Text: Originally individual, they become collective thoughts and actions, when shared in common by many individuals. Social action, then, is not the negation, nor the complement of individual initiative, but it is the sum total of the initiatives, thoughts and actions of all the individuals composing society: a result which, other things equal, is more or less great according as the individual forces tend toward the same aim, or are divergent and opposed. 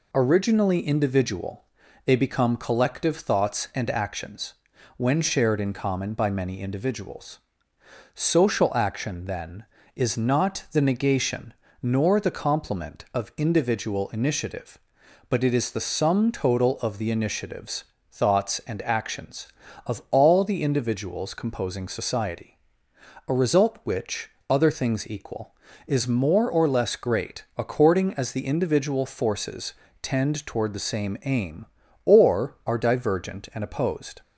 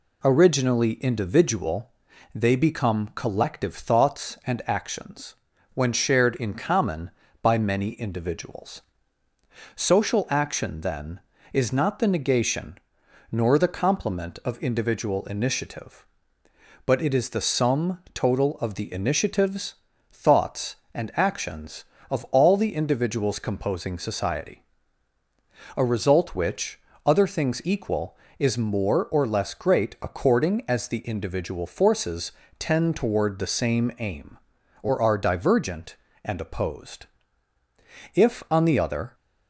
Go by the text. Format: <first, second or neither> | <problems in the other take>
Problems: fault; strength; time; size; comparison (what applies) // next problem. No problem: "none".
first | pauses between "forces" and "tend"; slight; at 32.3 s; 0.26 s long; slight in the first // goes on to say "If on the other"; noticeable; from 38.1 s on; 1.0 s long